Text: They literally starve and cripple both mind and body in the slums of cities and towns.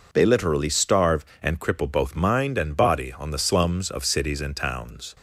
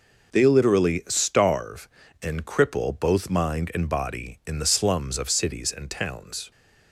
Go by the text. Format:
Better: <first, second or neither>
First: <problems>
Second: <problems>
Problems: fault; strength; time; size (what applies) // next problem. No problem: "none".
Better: second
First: says "on" for "in"; at 3.1 s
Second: none